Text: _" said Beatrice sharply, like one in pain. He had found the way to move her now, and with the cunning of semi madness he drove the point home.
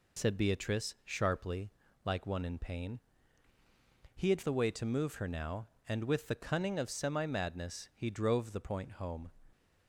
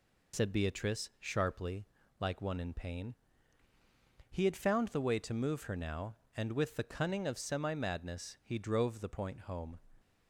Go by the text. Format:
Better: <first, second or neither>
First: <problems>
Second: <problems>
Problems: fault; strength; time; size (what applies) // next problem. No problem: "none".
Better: second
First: skips "found"; at 4.4 s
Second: none